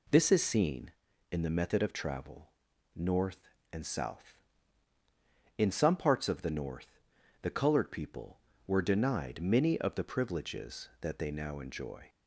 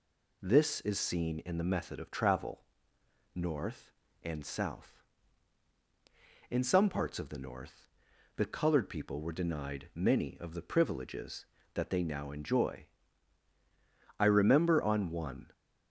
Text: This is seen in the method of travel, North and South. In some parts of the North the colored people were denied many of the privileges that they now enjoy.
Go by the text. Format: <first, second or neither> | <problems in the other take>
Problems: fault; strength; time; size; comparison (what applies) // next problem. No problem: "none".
first | pauses between "North" and "the"; noticeable; at 7.8 s; 0.48 s long; also in the first // goes on to say "I remember on one"; from 14.1 s on; 1.3 s long